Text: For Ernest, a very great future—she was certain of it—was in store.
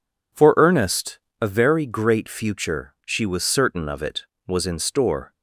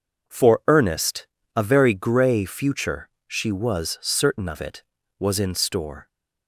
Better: first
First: none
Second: says "grey" for "great"; at 1.9 s

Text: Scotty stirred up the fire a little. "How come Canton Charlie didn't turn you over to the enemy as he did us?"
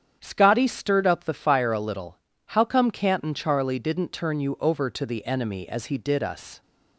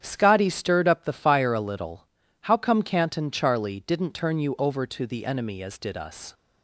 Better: first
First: starts louder than the rest; strong; until 1.2 s; 8.5 dB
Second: starts louder than the rest; strong; until 1.0 s; 9 dB // skips "he"; at 5.7 s

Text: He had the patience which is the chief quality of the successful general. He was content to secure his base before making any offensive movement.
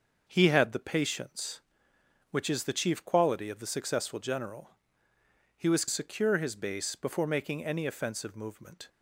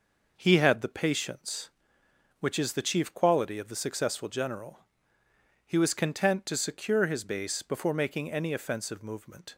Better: second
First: starts louder than the rest; until 1.2 s; 6.5 dB // skips "content to"; at 5.8 s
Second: none

